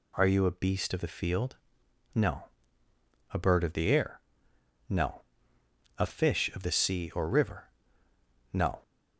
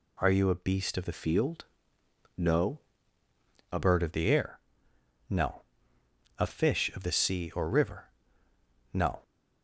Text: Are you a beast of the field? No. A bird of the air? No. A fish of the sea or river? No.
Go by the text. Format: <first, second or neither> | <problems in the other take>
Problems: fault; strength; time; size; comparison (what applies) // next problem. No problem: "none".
first | changes voice from "field" to "A"; from 1.1 to 3.7 s; 2.6 s long